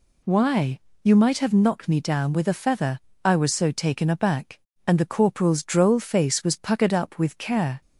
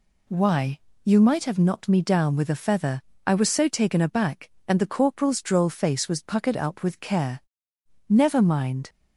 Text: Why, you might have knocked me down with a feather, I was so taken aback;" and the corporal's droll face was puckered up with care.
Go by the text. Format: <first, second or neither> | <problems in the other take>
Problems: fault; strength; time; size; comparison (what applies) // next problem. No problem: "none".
first | goes on to say "Never mind"; noticeable; from 8.0 s on; 0.80 s long